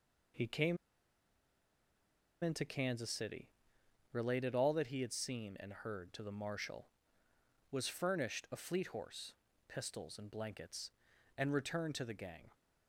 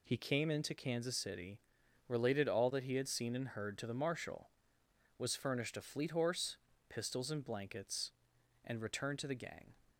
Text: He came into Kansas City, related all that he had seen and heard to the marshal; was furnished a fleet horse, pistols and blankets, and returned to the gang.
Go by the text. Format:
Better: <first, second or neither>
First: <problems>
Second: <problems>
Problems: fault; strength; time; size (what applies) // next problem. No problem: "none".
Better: second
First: pauses between "came" and "into"; strong; at 0.7 s; 1.6 s long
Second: none